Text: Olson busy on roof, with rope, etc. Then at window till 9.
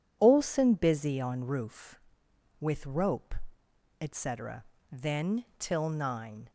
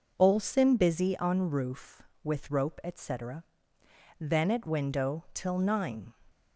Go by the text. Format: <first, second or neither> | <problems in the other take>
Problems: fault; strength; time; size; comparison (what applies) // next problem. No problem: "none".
second | skips "at window"; at 5.5 s